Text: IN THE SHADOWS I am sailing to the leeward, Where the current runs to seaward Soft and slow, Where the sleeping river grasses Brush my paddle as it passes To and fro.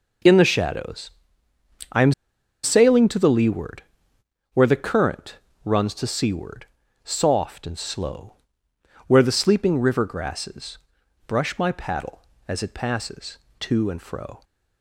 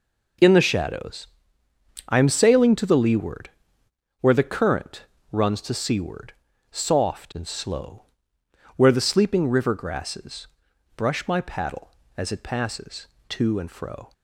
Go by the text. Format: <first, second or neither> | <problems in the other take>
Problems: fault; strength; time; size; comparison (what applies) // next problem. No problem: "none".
second | pauses between "SHADOWS" and "I"; noticeable; at 1.0 s; 0.82 s long; noticeable in the second // pauses between "am" and "sailing"; noticeable; at 2.1 s; 0.51 s long // pauses between "current" and "runs"; slight; at 5.3 s; 0.30 s long; slight in the second // pauses between "seaward" and "Soft"; at 6.6 s; 0.38 s long; also in the second // pauses between "grasses" and "Brush"; noticeable; at 10.7 s; 0.50 s long; noticeable in the second